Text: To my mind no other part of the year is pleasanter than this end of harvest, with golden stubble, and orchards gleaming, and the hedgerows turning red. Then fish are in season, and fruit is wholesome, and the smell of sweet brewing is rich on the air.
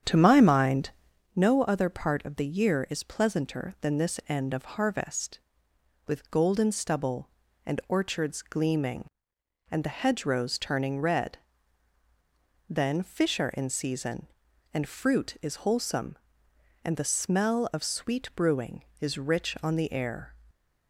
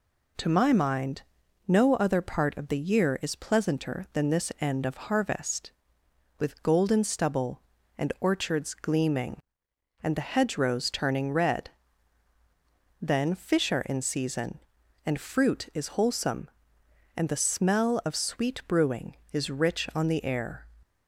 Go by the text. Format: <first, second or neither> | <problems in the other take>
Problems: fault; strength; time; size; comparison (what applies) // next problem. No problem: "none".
second | starts louder than the rest; strong; until 1.2 s; 8.5 dB // pauses between "mind" and "no"; at 0.9 s; 0.44 s long; also in the second